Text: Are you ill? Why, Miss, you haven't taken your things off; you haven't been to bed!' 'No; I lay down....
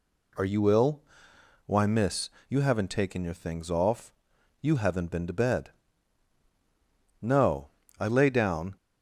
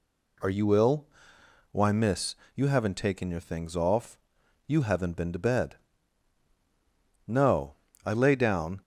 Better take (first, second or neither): neither